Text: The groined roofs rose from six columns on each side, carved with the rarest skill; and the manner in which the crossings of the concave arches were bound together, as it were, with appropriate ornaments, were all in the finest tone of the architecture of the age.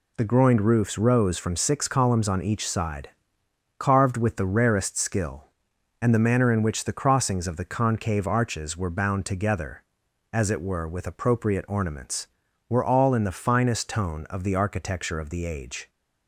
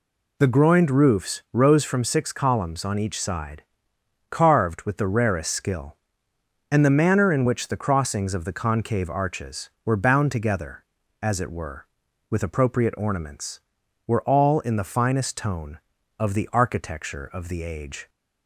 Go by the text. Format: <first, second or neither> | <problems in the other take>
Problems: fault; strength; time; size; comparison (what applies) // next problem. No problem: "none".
neither | none